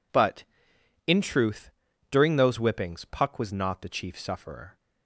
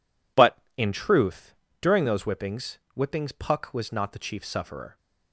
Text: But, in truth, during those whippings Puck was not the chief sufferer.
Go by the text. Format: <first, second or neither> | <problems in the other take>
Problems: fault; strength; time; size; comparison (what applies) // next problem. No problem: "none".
first | says "whippings" twice; at 2.9 s